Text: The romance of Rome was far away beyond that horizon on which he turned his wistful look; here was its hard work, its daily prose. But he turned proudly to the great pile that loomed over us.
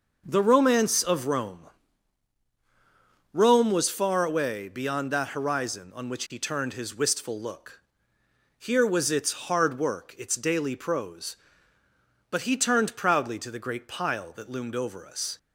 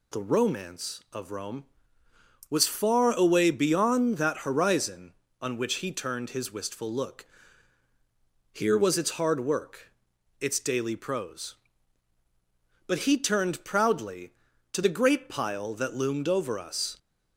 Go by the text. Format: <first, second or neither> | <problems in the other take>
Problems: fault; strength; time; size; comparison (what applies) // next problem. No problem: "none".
second | says "Rome" twice; at 3.3 s